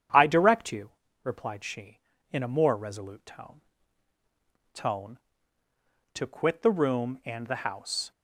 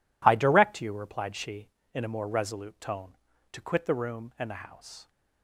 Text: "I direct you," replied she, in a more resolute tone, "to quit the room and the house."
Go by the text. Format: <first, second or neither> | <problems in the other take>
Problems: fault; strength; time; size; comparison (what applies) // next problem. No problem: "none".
second | starts louder than the rest; strong; until 1.4 s; 8.5 dB // says "tone" twice; at 4.7 s